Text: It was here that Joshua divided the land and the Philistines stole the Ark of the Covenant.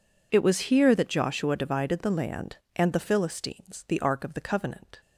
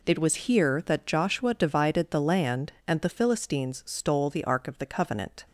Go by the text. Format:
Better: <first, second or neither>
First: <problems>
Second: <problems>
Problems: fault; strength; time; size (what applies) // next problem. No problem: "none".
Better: second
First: skips "stole"; at 3.8 s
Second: none